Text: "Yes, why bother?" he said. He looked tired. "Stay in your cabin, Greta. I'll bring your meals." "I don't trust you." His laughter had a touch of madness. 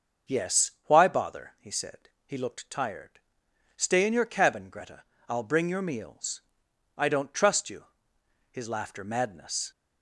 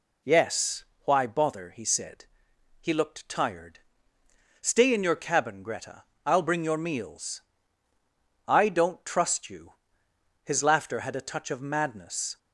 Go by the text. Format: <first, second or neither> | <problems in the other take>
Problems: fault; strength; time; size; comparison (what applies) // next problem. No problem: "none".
second | starts louder than the rest; until 1.4 s; 6 dB // skips "had a touch of"; at 9.0 s